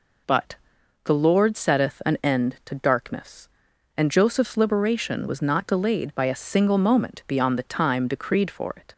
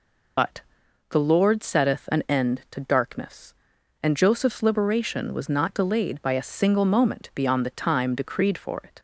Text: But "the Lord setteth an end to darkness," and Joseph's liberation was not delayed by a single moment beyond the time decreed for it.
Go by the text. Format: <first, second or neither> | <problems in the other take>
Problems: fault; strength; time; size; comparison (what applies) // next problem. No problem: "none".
first | loses the start of "But"; at 0.3 s; 55 ms // pauses between "But" and "the"; noticeable; at 0.6 s; 0.48 s long; noticeable in the first